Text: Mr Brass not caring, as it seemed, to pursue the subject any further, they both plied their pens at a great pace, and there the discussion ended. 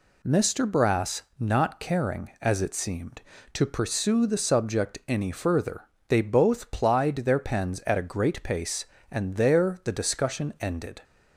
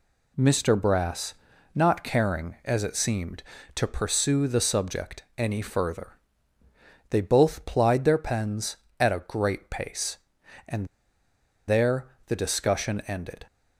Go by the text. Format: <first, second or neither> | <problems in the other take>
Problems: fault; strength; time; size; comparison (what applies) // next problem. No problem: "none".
first | pauses between "Brass" and "not"; at 1.3 s; 0.42 s long; slight in the first // pauses between "and" and "there"; noticeable; at 10.8 s; 0.80 s long // pauses between "there" and "the"; slight; at 12.0 s; 0.20 s long